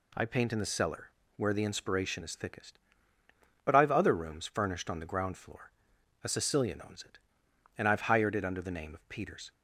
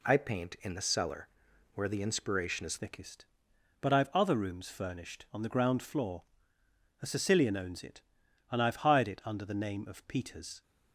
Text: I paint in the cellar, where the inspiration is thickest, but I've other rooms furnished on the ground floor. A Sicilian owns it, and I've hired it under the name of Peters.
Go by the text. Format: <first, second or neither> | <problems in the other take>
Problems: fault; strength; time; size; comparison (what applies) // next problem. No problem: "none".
first | changes voice at "thickest"; from 2.7 s on; 7.9 s long